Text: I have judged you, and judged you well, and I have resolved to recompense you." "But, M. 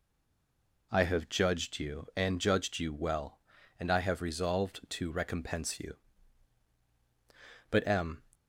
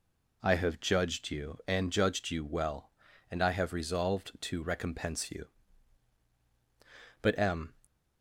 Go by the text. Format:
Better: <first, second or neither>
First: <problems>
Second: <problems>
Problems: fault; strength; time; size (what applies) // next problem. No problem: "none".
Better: second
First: stays silent before the first word; slight; until 0.9 s; 0.9 s long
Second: none